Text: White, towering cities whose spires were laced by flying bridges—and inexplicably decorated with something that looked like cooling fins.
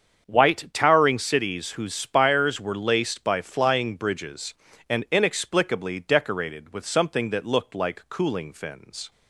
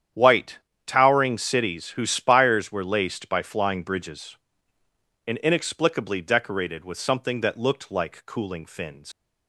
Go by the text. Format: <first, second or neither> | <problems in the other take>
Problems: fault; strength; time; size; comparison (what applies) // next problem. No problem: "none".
first | starts louder than the rest; strong; until 1.4 s; 9 dB; also in the first // leaves "fins" unfinished; at 9.1 s; 120 ms